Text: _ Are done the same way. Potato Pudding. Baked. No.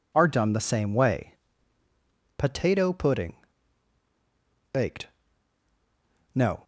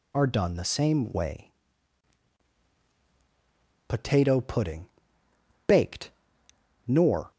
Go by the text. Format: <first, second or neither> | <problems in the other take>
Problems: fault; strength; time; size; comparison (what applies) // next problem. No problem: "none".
first | says "Nor" for "No"; at 6.8 s